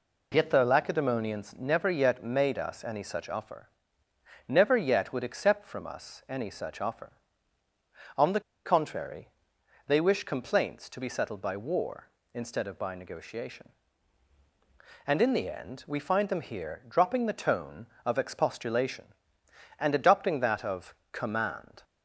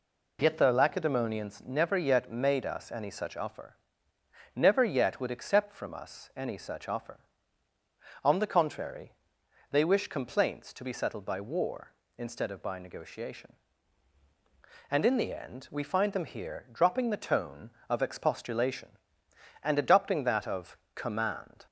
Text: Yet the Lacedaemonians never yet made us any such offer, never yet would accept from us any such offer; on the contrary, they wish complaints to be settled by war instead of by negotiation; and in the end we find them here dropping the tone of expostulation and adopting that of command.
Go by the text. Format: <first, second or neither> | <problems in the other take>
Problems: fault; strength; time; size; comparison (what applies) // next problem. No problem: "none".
second | pauses between "the" and "contrary"; slight; at 8.4 s; 0.24 s long // pauses between "of" and "command"; slight; at 20.9 s; 0.18 s long; slight in the second